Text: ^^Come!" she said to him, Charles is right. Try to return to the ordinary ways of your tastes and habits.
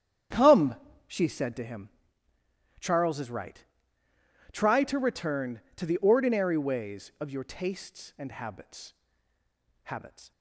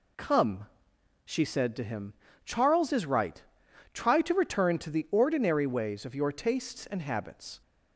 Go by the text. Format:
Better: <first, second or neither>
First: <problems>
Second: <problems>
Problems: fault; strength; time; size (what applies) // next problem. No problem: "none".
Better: second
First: starts louder than the rest; strong; until 1.6 s; 9 dB // says "habits" twice; at 9.8 s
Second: none